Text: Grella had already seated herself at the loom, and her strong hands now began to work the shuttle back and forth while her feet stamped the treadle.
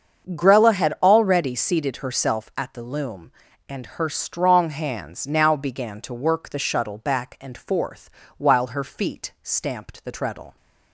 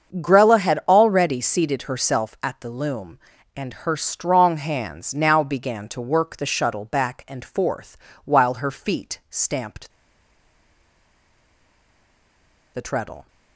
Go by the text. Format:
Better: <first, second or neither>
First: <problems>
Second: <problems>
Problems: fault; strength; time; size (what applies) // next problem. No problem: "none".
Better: first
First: starts louder than the rest; until 1.3 s; 7 dB // pauses between "forth" and "while"; slight; at 8.0 s; 0.30 s long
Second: starts louder than the rest; until 1.2 s; 7 dB // pauses between "forth" and "while"; slight; at 7.9 s; 0.30 s long // pauses between "stamped" and "the"; strong; at 9.9 s; 2.8 s long